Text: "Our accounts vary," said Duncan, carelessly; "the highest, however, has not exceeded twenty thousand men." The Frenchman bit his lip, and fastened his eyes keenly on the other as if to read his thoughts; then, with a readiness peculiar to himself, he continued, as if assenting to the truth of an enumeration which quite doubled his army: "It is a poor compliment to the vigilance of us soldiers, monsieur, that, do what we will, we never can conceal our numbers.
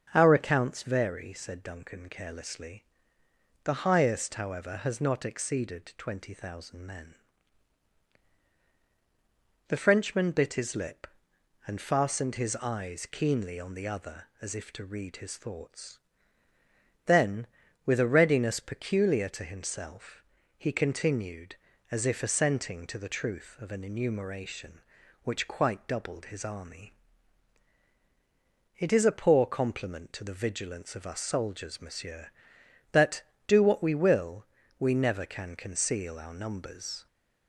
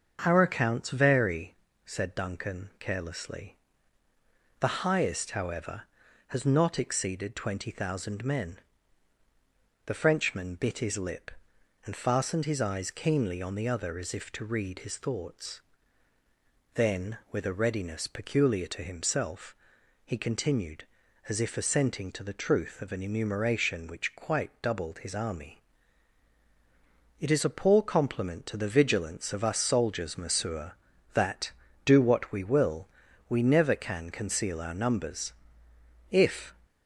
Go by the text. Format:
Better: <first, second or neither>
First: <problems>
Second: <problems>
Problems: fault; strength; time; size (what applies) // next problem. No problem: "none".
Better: first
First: starts louder than the rest; until 1.1 s; 6.5 dB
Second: starts louder than the rest; strong; until 1.2 s; 7 dB // goes on to say "If"; slight; from 36.1 s on; 0.42 s long